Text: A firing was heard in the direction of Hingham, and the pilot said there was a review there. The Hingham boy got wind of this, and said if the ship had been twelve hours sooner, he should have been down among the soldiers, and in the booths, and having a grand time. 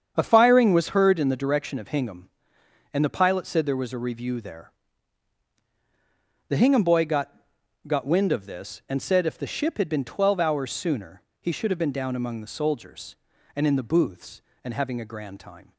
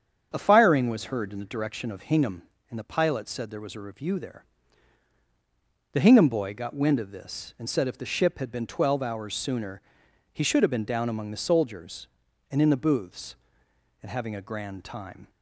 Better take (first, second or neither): second